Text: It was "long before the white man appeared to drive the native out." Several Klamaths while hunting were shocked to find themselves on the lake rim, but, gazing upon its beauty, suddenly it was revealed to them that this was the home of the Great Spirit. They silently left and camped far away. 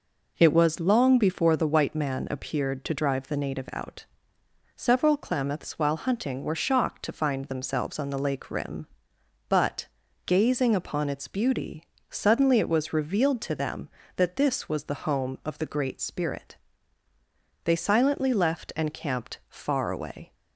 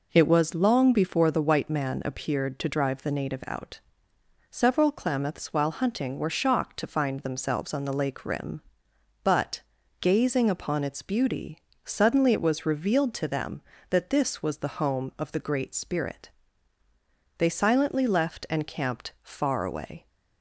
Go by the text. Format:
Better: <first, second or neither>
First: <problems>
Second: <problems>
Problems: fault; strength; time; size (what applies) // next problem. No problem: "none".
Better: neither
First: none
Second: none